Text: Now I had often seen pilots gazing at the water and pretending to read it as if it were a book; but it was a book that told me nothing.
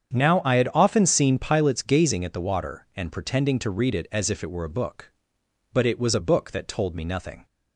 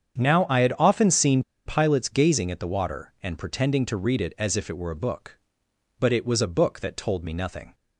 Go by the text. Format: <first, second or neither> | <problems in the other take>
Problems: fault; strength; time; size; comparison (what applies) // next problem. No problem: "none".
first | starts louder than the rest; strong; until 1.2 s; 8 dB; strong in the first // pauses between "seen" and "pilots"; slight; at 1.4 s; 0.23 s long